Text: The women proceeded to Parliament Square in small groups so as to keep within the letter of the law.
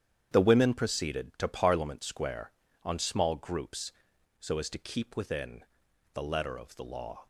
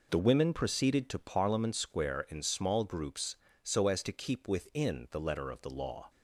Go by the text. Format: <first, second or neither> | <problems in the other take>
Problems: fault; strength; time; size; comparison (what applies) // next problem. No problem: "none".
second | starts louder than the rest; strong; until 1.3 s; 9 dB // says "on" for "in"; at 2.8 s // pauses between "within" and "the"; noticeable; at 5.6 s; 0.52 s long